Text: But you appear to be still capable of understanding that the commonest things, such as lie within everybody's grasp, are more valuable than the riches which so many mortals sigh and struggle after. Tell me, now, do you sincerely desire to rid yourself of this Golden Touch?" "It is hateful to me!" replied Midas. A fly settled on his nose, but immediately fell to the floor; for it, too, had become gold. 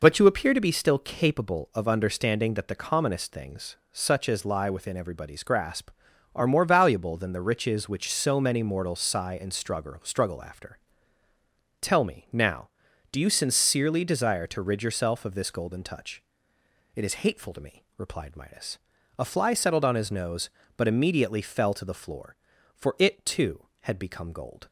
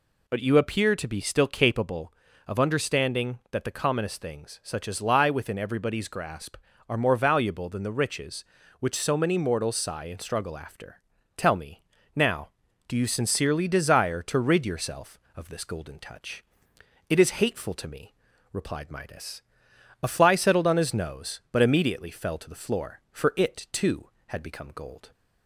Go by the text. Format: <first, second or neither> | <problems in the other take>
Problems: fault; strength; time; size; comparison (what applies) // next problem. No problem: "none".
second | says "struggle" twice; at 10.0 s